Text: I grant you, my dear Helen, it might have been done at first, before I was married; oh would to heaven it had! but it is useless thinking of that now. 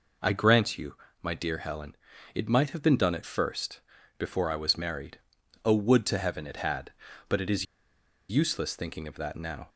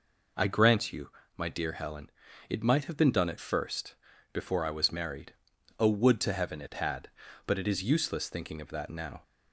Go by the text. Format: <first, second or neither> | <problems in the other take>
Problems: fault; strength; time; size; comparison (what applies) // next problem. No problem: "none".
second | pauses between "is" and "useless"; noticeable; at 7.6 s; 0.64 s long